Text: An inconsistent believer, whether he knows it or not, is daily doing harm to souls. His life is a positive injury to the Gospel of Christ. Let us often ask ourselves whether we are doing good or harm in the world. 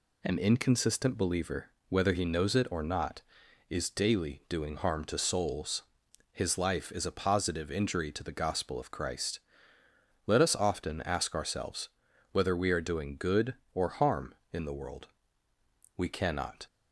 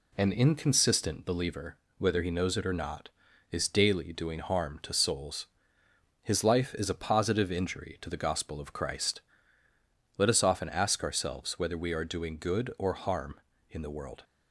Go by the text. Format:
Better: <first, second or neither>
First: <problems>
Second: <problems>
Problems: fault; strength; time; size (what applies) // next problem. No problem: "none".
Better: second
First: pauses between "ourselves" and "whether"; at 11.8 s; 0.44 s long // goes on to say "We cannot"; noticeable; from 15.9 s on; 0.70 s long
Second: none